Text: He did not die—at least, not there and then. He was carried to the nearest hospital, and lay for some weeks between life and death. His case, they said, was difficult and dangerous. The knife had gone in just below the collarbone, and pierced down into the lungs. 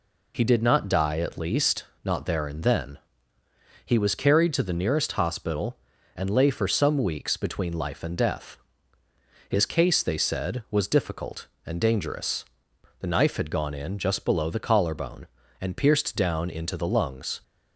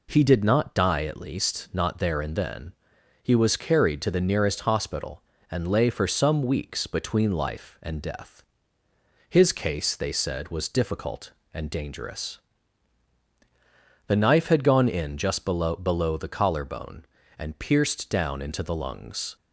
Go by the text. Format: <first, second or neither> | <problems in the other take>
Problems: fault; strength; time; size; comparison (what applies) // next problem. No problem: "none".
first | says "below" twice; at 15.7 s